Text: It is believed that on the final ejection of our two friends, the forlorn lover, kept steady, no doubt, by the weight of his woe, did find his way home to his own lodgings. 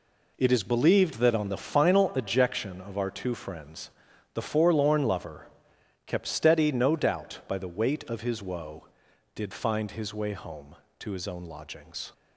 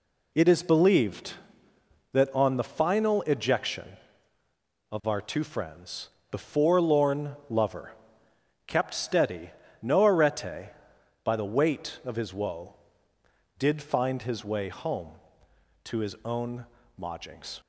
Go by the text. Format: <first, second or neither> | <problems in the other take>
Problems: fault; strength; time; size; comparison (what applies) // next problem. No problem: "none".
first | says "arete" for "doubt"; at 10.0 s // pauses between "own" and "lodgings"; slight; at 16.6 s; 0.32 s long